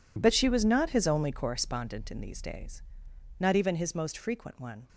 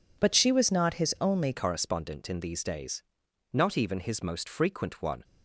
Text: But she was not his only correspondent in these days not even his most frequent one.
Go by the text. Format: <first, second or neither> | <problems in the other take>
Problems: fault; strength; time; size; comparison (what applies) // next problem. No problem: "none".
first | changes voice at "correspondent"; from 1.5 s on; 3.7 s long // pauses between "days" and "not"; noticeable; at 3.0 s; 0.54 s long; noticeable in the first